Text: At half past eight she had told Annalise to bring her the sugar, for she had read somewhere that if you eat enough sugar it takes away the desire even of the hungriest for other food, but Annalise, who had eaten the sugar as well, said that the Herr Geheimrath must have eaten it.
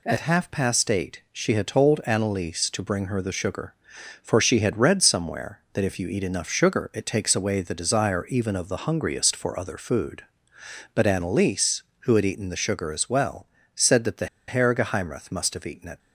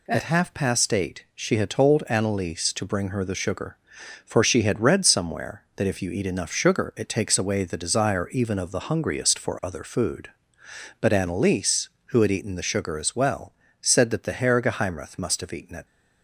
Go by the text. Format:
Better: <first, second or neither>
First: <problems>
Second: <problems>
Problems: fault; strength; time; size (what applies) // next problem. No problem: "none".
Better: second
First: pauses between "the" and "Herr"; slight; at 14.2 s; 0.20 s long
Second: none